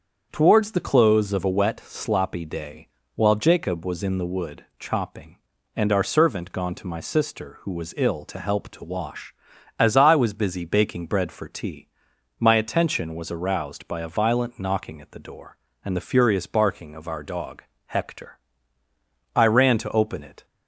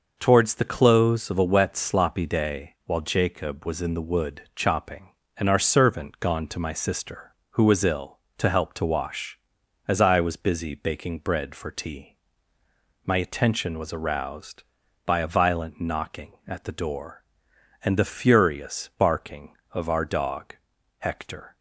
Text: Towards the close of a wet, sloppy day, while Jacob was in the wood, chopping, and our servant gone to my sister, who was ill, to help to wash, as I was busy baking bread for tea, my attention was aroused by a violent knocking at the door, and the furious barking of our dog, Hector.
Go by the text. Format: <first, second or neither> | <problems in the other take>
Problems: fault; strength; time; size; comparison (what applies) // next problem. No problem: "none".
second | starts louder than the rest; strong; until 1.3 s; 7 dB // goes on to say "I ran to open it"; noticeable; from 19.3 s on; 1.1 s long